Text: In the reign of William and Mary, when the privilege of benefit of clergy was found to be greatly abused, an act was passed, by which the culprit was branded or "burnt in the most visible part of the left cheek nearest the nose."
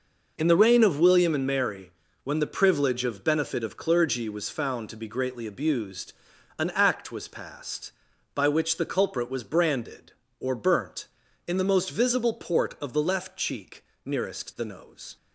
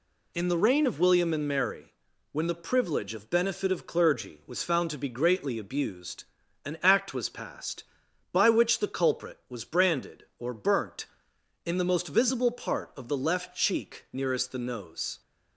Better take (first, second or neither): second